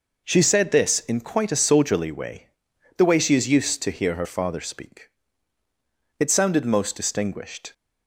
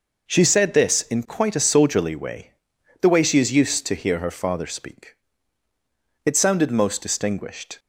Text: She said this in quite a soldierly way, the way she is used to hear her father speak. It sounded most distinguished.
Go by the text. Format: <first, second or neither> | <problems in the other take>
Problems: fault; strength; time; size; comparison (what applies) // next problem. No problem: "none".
neither | none